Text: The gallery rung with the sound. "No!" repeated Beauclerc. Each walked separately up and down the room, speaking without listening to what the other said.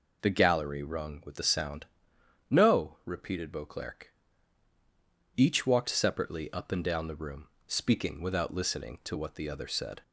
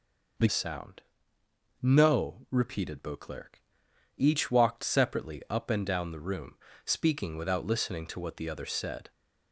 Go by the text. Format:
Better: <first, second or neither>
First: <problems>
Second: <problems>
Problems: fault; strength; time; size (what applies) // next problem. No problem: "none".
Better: first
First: none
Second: skips "gallery rung with the"; at 0.4 s